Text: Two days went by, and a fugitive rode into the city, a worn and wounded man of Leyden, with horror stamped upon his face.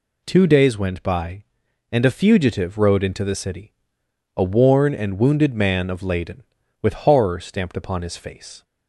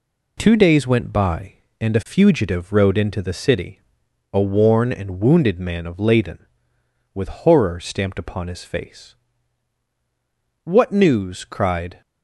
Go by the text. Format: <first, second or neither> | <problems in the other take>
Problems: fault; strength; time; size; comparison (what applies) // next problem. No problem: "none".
first | goes on to say "What news cried"; from 10.6 s on; 1.3 s long